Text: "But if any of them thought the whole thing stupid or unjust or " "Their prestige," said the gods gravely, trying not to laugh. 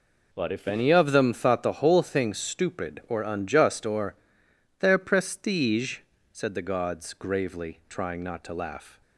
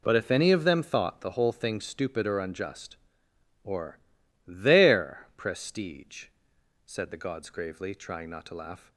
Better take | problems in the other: neither | none

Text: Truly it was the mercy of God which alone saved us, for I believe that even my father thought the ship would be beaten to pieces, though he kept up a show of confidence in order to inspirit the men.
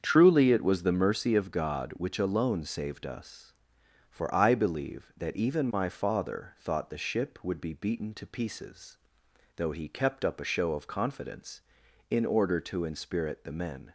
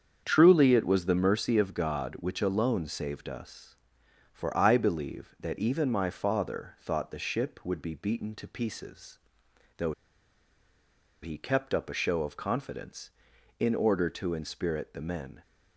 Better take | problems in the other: first | starts louder than the rest; strong; until 1.2 s; 7.5 dB; strong in the first // pauses between "though" and "he"; strong; at 9.9 s; 1.3 s long

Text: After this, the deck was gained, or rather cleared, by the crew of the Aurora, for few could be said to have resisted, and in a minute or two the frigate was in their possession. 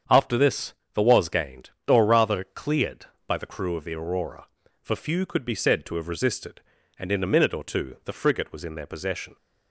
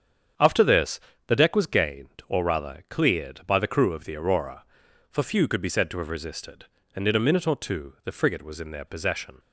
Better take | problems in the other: second | starts louder than the rest; strong; until 1.3 s; 7.5 dB; strong in the second // skips "deck"; at 1.0 s

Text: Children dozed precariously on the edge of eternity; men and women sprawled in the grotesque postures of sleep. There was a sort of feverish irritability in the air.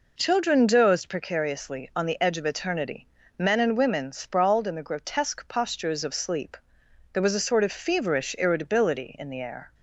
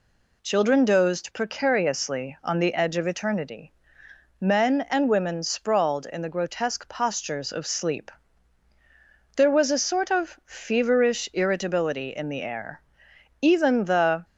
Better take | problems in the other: first | goes on to say "Even the"; noticeable; from 13.4 s on; 0.82 s long

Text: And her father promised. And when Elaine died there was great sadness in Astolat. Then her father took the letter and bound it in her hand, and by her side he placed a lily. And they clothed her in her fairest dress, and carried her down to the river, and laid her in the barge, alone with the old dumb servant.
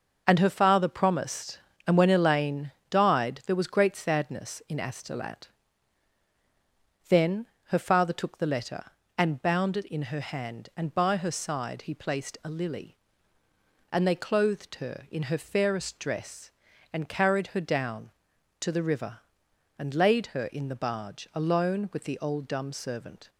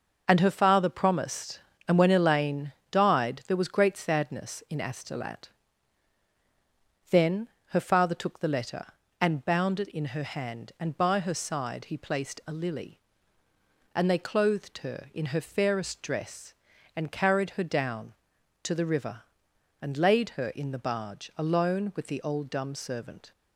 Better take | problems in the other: neither | pauses between "Elaine" and "died"; slight; the same in both // pauses between "Then" and "her"; slight; the same in both

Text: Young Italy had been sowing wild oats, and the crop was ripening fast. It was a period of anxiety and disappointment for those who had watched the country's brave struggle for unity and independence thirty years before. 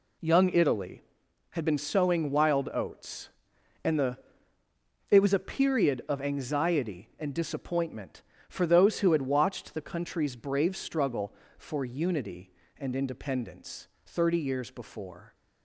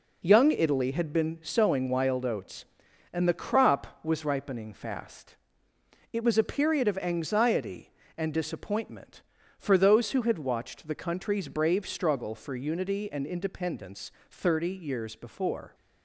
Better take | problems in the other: second | skips "crop was ripening fast"; at 4.6 s // pauses between "independence" and "thirty"; slight; at 13.8 s; 0.18 s long; slight in the second

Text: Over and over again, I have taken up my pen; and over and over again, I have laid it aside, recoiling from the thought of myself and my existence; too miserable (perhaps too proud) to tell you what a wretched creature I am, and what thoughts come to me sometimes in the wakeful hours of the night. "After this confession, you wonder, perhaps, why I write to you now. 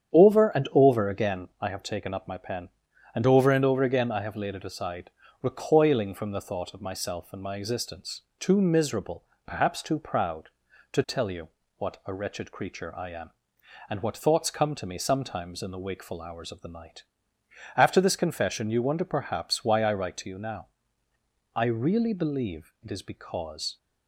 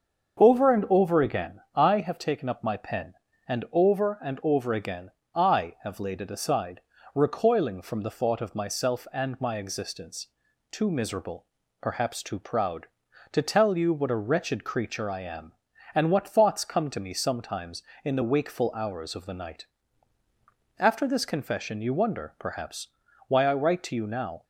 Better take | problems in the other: second | starts louder than the rest; strong; until 1.2 s; 9 dB; also in the second // pauses between "you" and "what"; slight; at 11.4 s; 0.30 s long // goes on to say "I really believe it is because"; strong; from 21.5 s on; 2.2 s long

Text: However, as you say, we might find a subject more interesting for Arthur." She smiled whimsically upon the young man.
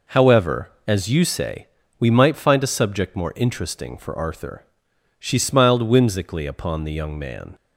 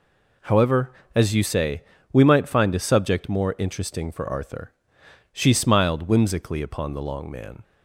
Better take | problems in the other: first | says "long" for "young"; at 7.0 s

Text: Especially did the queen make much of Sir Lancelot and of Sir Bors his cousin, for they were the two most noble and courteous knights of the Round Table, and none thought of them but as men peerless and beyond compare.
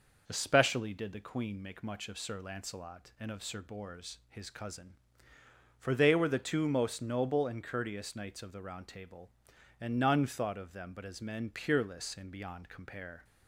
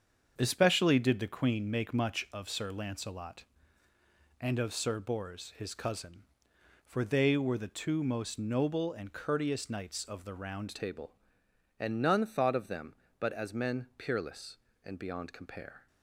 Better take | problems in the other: first | starts louder than the rest; strong; until 1.3 s; 7 dB // changes voice at "Table"; from 10.7 s on; 5.1 s long

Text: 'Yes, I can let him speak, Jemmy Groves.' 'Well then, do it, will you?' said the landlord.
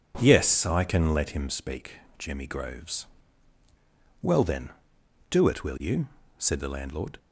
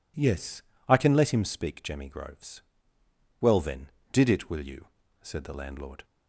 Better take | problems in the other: first | says "did" for "do"; at 4.1 s

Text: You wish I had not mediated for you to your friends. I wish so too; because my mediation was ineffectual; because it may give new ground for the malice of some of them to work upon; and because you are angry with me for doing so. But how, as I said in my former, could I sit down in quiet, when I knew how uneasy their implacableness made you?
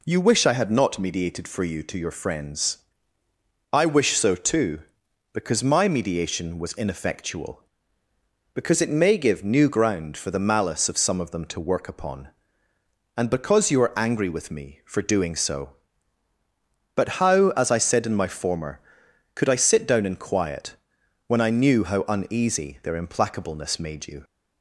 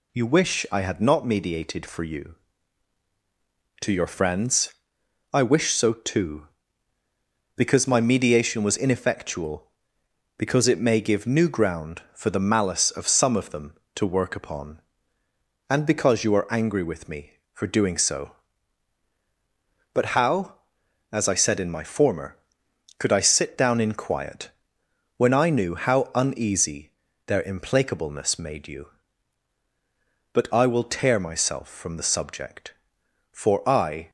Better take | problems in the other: first | pauses between "uneasy" and "their"; at 26.8 s; 0.38 s long // goes on to say "But I will tear myself from the subject for I"; strong; from 30.3 s on; 3.7 s long

